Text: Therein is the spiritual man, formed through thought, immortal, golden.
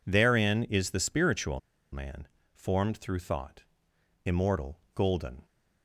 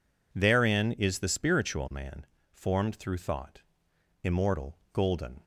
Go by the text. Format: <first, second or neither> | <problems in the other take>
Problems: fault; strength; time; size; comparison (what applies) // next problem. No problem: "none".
second | pauses between "spiritual" and "man"; slight; at 1.5 s; 0.33 s long